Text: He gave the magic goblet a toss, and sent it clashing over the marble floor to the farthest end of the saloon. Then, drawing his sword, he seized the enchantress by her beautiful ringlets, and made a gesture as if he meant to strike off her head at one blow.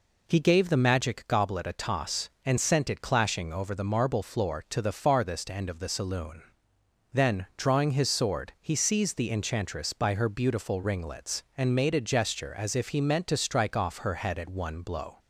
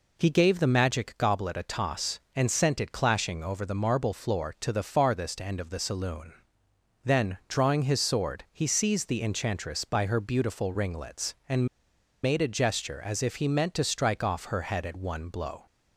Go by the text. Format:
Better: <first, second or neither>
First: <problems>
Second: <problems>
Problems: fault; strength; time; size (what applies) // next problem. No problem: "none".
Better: first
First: none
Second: pauses between "and" and "made"; noticeable; at 11.6 s; 0.57 s long